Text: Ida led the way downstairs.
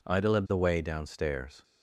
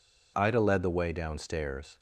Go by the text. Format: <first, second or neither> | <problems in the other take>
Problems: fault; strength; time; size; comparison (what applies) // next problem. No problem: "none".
neither | none